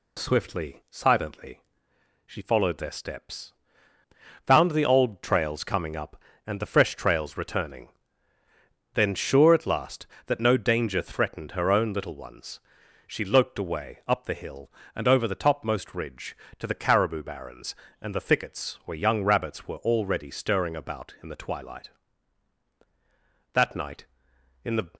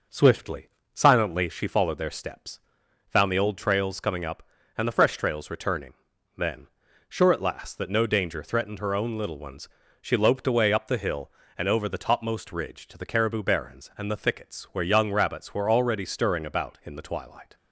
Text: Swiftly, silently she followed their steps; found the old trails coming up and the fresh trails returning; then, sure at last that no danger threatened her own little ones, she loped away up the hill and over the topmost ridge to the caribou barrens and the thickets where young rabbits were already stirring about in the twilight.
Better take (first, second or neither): second